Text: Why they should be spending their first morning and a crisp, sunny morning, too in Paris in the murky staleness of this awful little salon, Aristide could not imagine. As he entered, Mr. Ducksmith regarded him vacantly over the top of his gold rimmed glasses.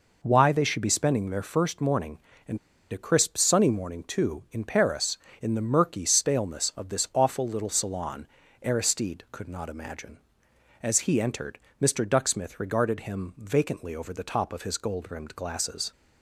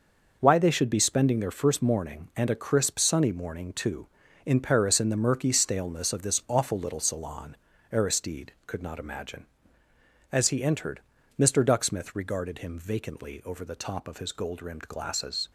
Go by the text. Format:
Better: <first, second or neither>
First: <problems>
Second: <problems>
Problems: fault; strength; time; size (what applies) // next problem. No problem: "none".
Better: second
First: pauses between "and" and "a"; slight; at 2.5 s; 0.34 s long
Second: none